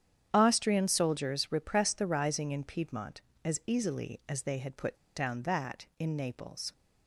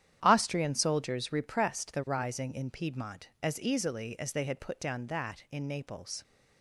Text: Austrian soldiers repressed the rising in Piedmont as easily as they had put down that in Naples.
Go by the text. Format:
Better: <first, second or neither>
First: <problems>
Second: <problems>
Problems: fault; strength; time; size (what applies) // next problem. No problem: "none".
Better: second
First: starts louder than the rest; strong; until 1.3 s; 9 dB // pauses between "put" and "down"; slight; at 4.9 s; 0.19 s long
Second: starts louder than the rest; strong; until 1.2 s; 10 dB